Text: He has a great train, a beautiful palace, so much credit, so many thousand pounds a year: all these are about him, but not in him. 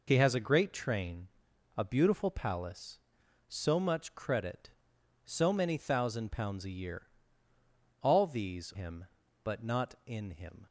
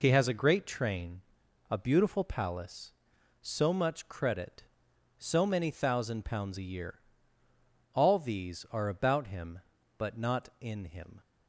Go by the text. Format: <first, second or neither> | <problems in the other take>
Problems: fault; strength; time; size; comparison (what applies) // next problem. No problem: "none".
second | skips "are about"; at 8.7 s